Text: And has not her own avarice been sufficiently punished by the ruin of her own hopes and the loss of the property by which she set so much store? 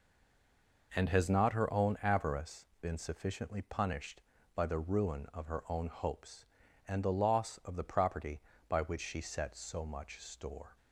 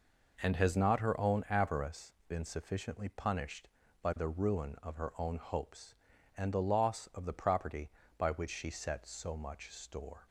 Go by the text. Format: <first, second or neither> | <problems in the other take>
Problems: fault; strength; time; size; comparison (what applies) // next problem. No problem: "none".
second | stays silent before the first word; slight; until 0.9 s; 0.9 s long // pauses between "avarice" and "been"; slight; at 2.6 s; 0.16 s long; slight in the second